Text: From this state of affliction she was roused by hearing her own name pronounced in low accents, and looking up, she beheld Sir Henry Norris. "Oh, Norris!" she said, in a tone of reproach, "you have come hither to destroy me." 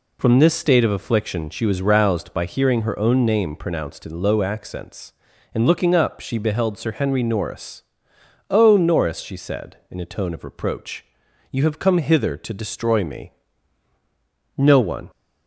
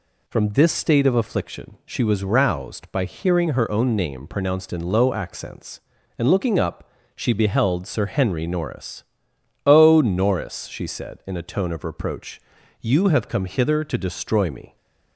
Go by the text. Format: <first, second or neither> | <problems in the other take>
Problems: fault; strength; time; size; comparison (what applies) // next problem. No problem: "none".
second | goes on to say "No one"; from 14.5 s on; 0.52 s long